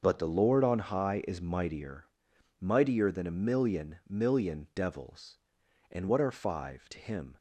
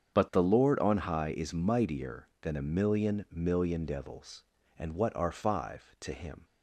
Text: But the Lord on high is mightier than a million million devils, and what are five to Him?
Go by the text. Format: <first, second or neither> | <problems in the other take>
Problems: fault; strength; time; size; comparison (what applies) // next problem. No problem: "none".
second | starts louder than the rest; until 1.0 s; 6.5 dB; strong in the second // says "mightier" twice; at 2.5 s